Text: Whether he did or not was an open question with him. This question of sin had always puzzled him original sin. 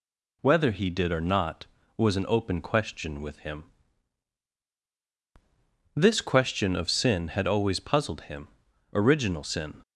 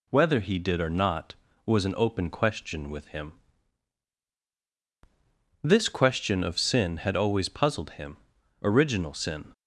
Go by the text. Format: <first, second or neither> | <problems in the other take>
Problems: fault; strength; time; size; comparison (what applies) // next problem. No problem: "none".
neither | pauses between "him" and "original"; noticeable; the same in both